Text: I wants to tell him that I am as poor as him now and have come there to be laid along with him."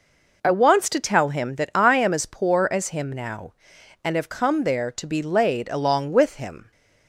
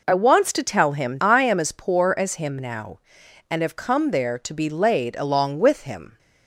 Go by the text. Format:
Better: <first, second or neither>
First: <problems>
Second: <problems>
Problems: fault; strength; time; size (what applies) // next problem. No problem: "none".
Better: first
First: none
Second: skips "that"; at 1.1 s